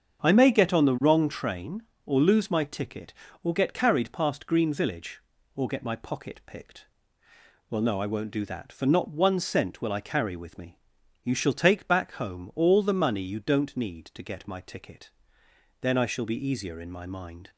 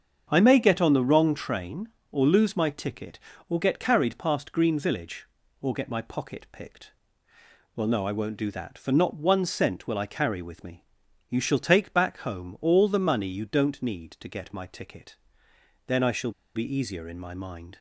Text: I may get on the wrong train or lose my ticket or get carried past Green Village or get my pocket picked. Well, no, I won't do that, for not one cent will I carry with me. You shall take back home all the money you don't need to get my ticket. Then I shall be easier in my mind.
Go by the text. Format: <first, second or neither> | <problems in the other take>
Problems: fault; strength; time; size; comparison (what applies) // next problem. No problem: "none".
first | starts louder than the rest; strong; until 1.3 s; 7 dB; strong in the first // pauses between "shall" and "be"; slight; at 16.3 s; 0.24 s long